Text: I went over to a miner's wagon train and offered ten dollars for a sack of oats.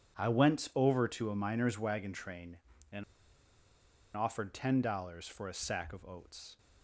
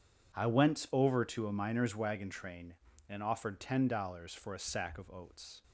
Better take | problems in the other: second | pauses between "and" and "offered"; at 3.0 s; 1.1 s long

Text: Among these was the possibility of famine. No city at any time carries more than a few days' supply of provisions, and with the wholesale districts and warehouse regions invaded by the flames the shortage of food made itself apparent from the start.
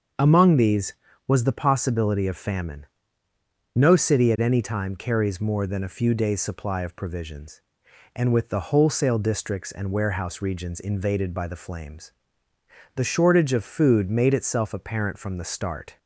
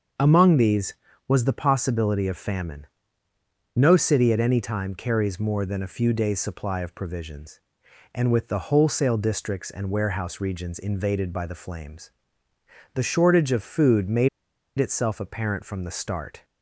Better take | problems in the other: first | starts louder than the rest; until 1.5 s; 6.5 dB; also in the first // pauses between "flames" and "the"; noticeable; at 12.1 s; 0.84 s long; noticeable in the first // pauses between "made" and "itself"; noticeable; at 14.2 s; 0.49 s long

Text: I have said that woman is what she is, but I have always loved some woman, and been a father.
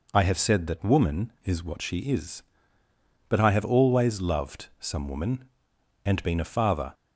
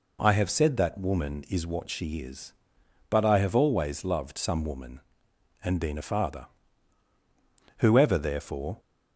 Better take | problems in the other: first | goes on to say "Whoever therefore"; noticeable; from 7.7 s on; 1.0 s long

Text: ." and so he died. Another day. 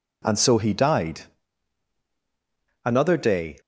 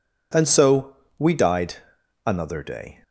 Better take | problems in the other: first | says "we" for "he"; at 1.1 s

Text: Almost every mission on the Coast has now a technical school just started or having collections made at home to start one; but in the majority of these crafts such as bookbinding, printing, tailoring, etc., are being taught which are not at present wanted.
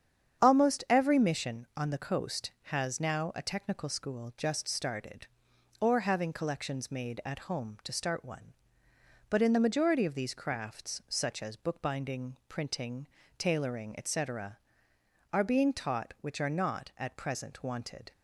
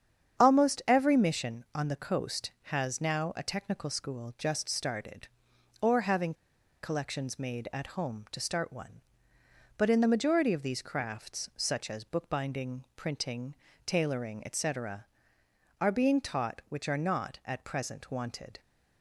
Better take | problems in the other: first | starts louder than the rest; strong; until 1.4 s; 8 dB; strong in the first // pauses between "having" and "collections"; noticeable; at 6.3 s; 0.47 s long

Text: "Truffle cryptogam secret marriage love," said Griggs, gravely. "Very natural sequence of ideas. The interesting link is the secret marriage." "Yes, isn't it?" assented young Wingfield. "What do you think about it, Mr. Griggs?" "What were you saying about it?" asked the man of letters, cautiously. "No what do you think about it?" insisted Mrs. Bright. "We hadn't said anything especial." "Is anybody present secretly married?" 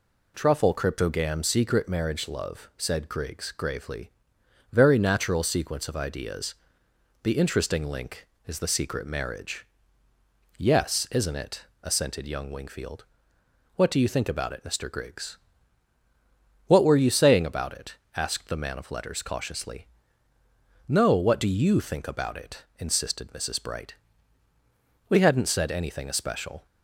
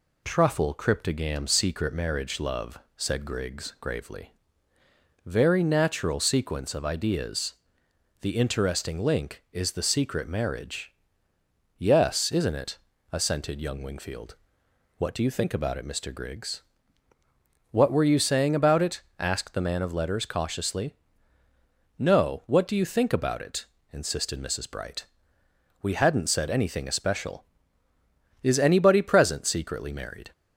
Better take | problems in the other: second | stops before "Is anybody present secretly married"; at 26.6 s

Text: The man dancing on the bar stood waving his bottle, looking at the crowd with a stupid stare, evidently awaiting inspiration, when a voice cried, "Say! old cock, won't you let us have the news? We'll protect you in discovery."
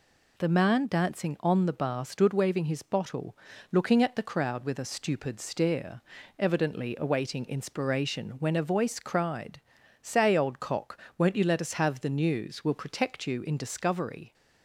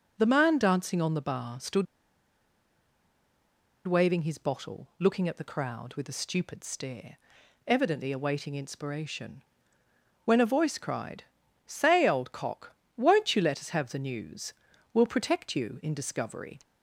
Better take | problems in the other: first | pauses between "stood" and "waving"; strong; at 1.8 s; 2.0 s long

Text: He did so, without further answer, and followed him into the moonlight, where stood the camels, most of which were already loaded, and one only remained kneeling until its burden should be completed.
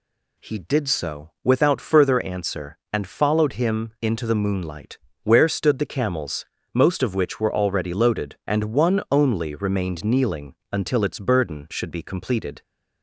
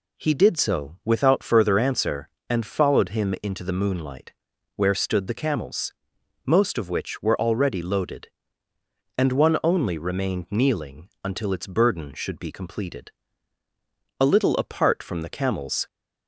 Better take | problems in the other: first | pauses between "kneeling" and "until"; slight; at 11.0 s; 0.16 s long; slight in the first // goes on to say "A little apart from the camels"; from 14.2 s on; 1.6 s long

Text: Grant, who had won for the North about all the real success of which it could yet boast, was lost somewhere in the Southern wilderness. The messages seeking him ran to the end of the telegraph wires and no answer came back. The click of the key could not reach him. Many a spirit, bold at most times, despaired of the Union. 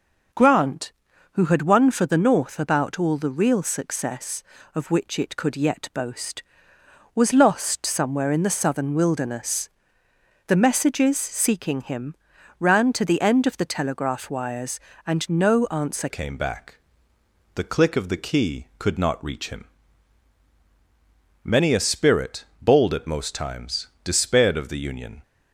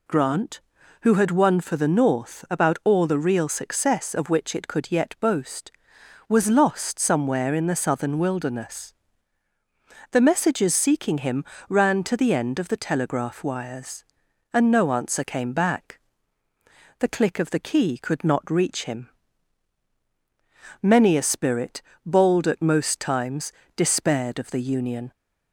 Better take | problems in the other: second | pauses between "him" and "ran"; noticeable; at 12.1 s; 0.46 s long; slight in the second // changes voice at "came"; from 16.0 s on; 9.2 s long

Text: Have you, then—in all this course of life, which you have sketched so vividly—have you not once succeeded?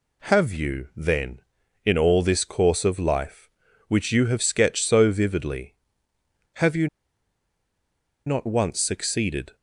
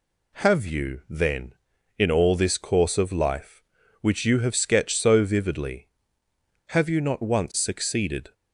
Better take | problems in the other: second | pauses between "you" and "not"; strong; at 6.8 s; 1.3 s long

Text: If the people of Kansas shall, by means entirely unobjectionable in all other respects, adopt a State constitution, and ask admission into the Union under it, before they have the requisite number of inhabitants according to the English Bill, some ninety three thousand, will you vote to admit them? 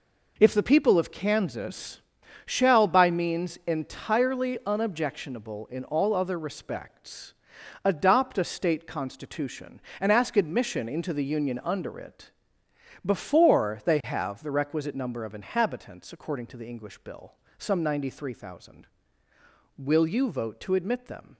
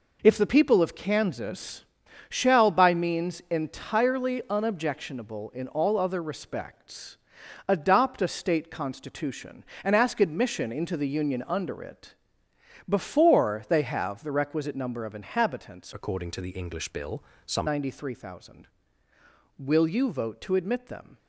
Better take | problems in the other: first | pauses between "Kansas" and "shall"; at 1.8 s; 0.42 s long; also in the first // changes voice from "according" to "some"; from 15.9 to 17.6 s; 1.7 s long

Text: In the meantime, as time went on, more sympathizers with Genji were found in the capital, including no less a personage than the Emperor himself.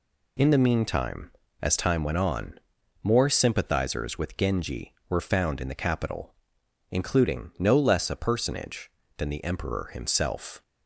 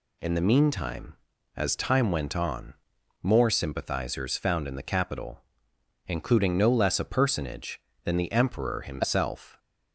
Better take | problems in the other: first | skips "with Genji were"; at 4.3 s

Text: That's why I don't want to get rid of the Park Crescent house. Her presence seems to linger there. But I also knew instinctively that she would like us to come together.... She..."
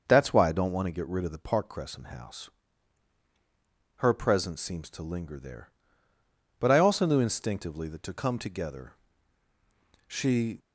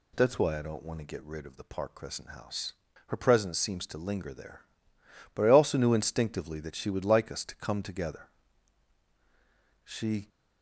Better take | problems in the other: second | starts louder than the rest; noticeable; until 1.0 s; 6 dB // skips "she would like us"; at 8.0 s

